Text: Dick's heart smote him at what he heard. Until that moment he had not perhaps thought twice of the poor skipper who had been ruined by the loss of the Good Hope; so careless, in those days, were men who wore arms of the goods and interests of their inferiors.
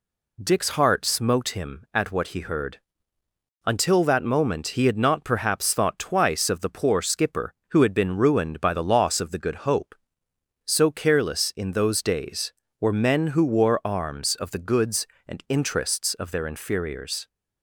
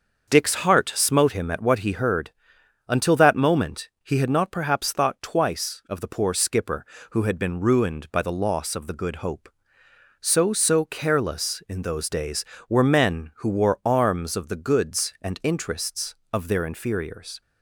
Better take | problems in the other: first | starts louder than the rest; until 1.3 s; 6.5 dB // says "so" twice; at 10.5 s

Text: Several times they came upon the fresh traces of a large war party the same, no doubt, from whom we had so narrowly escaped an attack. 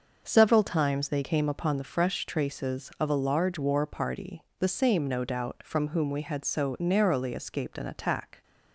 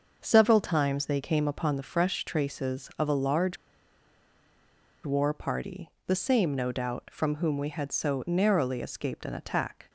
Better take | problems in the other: first | starts louder than the rest; until 1.2 s; 6 dB; also in the first // pauses between "large" and "war"; strong; at 3.5 s; 1.4 s long // pauses between "party" and "the"; slight; at 5.8 s; 0.16 s long; slight in the first

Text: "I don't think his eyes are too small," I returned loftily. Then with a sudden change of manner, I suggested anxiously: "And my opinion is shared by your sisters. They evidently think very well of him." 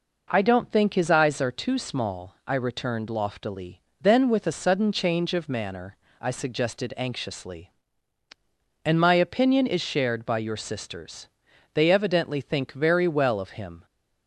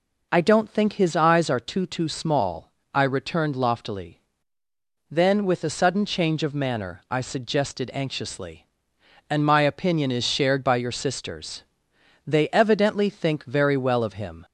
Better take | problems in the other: first | says "too" twice; at 1.8 s

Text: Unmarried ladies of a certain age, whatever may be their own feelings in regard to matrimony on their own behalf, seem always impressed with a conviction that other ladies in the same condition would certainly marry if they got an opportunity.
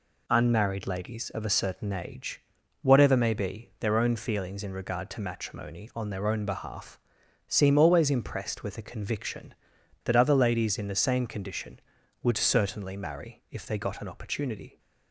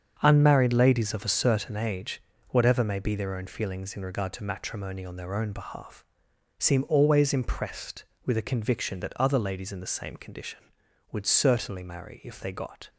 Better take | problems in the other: first | starts louder than the rest; until 1.2 s; 7 dB // stops before "an opportunity"; at 12.8 s

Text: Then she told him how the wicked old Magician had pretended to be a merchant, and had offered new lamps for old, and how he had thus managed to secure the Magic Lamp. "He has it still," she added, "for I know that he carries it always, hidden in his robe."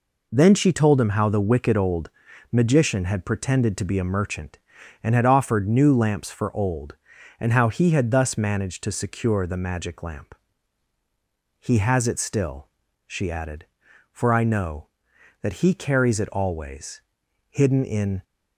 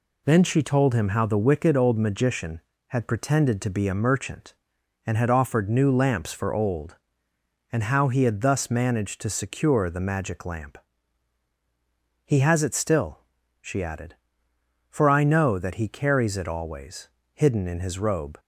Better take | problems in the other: second | pauses between "old" and "Magician"; at 2.0 s; 0.42 s long // stops before "his robe"; at 18.2 s

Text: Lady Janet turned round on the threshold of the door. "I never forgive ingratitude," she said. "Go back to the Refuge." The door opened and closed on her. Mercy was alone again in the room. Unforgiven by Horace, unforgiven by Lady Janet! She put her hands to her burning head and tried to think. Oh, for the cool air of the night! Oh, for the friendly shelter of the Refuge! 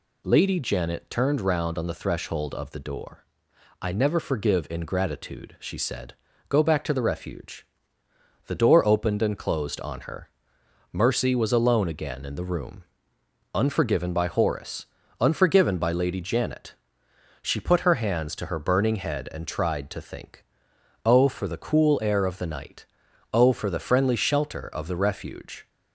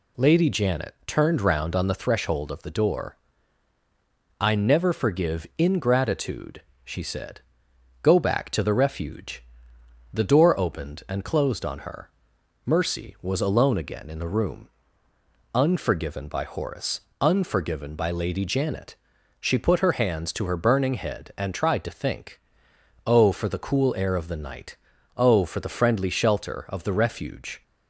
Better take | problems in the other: neither | none

